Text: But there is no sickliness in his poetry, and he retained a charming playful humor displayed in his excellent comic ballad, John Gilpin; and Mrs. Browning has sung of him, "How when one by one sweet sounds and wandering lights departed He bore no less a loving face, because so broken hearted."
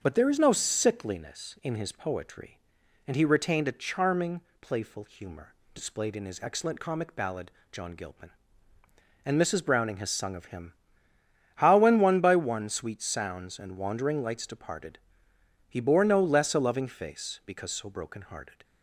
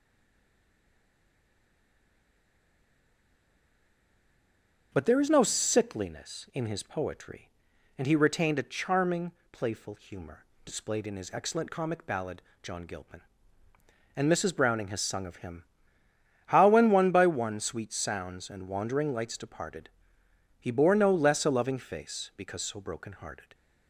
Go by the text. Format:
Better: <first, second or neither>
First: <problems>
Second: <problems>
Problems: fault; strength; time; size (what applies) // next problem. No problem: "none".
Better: first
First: starts louder than the rest; until 1.0 s; 7 dB // pauses between "charming" and "playful"; slight; at 4.4 s; 0.20 s long // pauses between "humor" and "displayed"; slight; at 5.5 s; 0.18 s long // pauses between "departed" and "He"; noticeable; at 14.9 s; 0.68 s long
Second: stays silent before the first word; strong; until 4.9 s; 4.9 s long // starts louder than the rest; until 5.9 s; 6.5 dB // pauses between "charming" and "playful"; slight; at 9.3 s; 0.20 s long // pauses between "humor" and "displayed"; slight; at 10.4 s; 0.18 s long // pauses between "departed" and "He"; noticeable; at 19.8 s; 0.68 s long